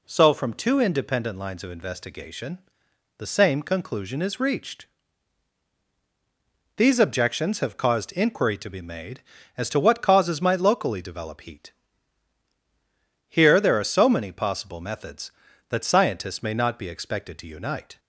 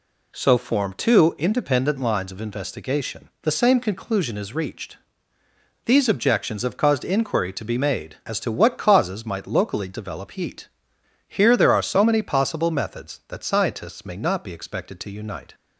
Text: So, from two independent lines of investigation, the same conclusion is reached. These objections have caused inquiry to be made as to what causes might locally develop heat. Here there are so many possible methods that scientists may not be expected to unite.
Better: first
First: none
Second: says "form" for "from"; at 0.5 s

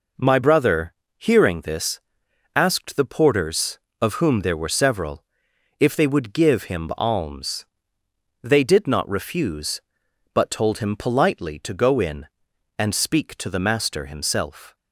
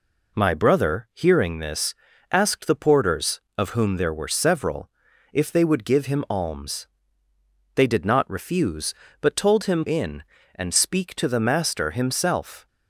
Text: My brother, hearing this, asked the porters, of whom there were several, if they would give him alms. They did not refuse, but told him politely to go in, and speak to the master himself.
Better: first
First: none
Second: skips "politely to go"; at 9.8 s

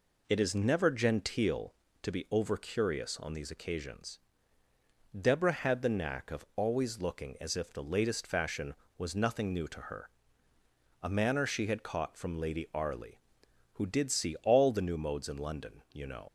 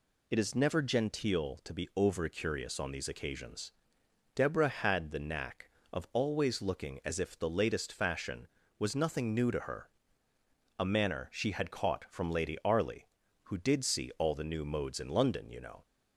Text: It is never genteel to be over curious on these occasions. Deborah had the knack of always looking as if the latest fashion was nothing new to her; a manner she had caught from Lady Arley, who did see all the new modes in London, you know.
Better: second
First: leaves "know" unfinished; at 16.2 s; 65 ms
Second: none

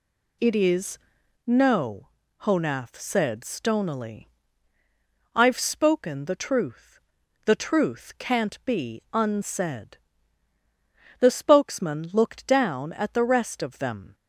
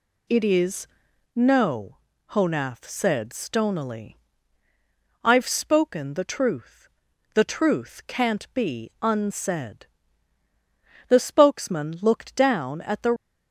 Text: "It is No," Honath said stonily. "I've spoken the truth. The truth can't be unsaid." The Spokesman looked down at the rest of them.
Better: first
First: pauses between "is" and "No"; noticeable; at 0.9 s; 0.46 s long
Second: pauses between "is" and "No"; noticeable; at 0.8 s; 0.46 s long // stops before "rest of them"; at 13.1 s

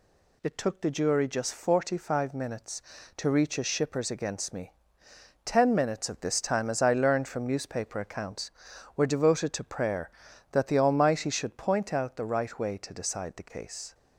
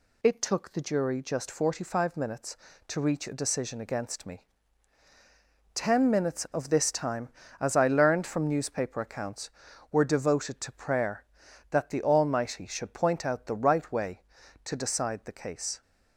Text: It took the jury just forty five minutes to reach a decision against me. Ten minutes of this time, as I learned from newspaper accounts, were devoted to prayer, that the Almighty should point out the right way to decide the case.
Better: second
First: says "shippers" for "decision"; at 3.6 s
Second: none

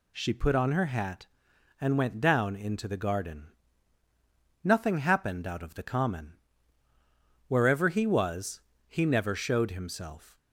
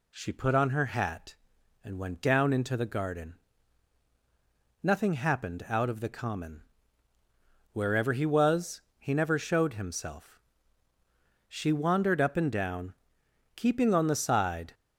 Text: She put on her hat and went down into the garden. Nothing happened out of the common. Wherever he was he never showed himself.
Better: first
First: pauses between "was" and "he"; slight; at 8.6 s; 0.26 s long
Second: pauses between "was" and "he"; slight; at 8.7 s; 0.20 s long // goes on to say "She wandered up and down keeping on the side"; strong; from 11.4 s on; 3.2 s long

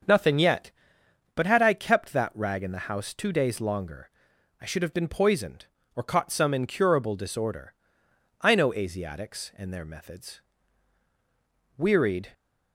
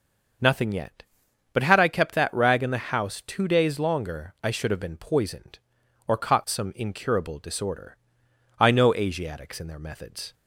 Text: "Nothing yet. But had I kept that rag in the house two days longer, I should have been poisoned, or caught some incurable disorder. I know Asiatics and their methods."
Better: second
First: starts louder than the rest; until 1.7 s; 7 dB // goes on to say "Wearied"; from 11.7 s on; 0.54 s long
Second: starts louder than the rest; noticeable; until 1.9 s; 6 dB

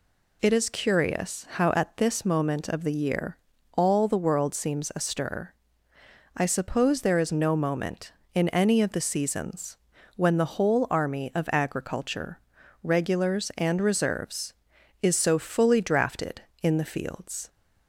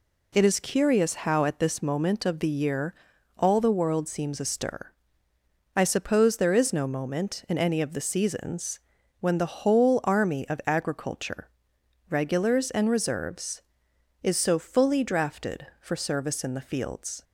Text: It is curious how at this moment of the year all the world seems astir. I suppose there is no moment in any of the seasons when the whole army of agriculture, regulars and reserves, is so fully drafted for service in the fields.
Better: second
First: pauses between "year" and "all"; at 3.3 s; 0.38 s long // pauses between "seasons" and "when"; slight; at 9.7 s; 0.36 s long // skips "for service"; at 16.5 s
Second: pauses between "year" and "all"; at 2.9 s; 0.42 s long // pauses between "seasons" and "when"; at 8.7 s; 0.40 s long

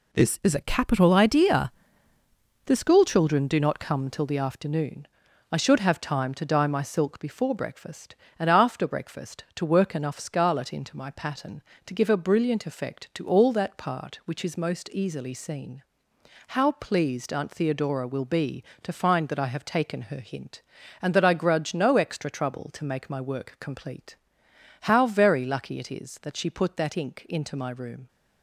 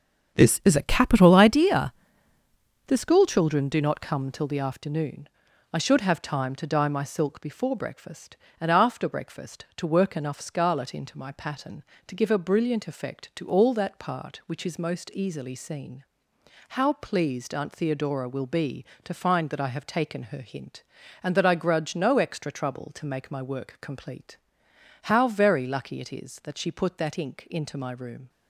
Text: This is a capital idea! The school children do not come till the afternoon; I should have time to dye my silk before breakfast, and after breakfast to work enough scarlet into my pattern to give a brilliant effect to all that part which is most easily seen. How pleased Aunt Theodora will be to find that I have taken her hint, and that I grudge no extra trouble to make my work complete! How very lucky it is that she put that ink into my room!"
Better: first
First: none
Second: starts louder than the rest; until 1.6 s; 6.5 dB

